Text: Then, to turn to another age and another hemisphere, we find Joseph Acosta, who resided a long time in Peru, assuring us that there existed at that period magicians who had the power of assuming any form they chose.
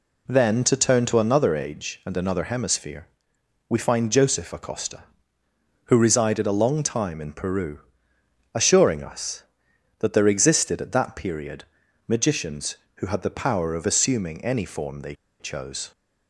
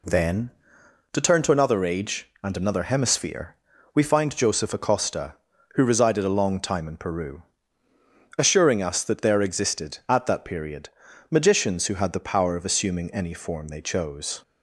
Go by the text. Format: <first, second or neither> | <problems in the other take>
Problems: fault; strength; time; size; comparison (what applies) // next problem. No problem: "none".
second | pauses between "period" and "magicians"; at 11.6 s; 0.42 s long; also in the second // pauses between "they" and "chose"; slight; at 15.1 s; 0.26 s long